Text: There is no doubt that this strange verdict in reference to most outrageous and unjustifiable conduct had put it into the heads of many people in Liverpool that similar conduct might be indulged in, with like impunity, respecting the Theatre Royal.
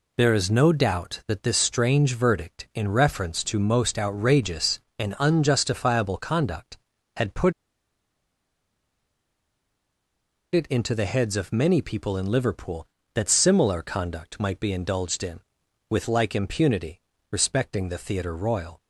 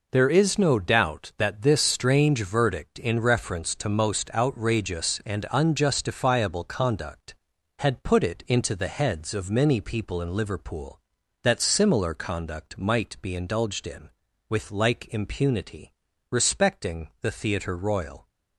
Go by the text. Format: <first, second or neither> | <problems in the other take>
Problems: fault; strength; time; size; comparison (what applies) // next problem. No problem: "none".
second | pauses between "put" and "it"; strong; at 7.5 s; 3.0 s long